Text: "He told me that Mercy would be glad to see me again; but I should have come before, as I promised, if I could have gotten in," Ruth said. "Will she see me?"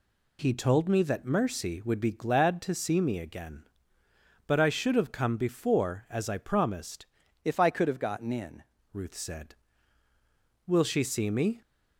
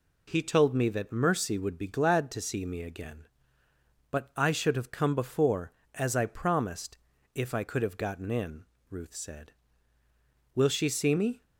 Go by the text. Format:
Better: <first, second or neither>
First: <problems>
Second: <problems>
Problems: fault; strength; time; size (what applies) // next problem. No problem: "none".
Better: second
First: changes voice from "if" to "in"; from 7.4 to 8.6 s; 1.2 s long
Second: none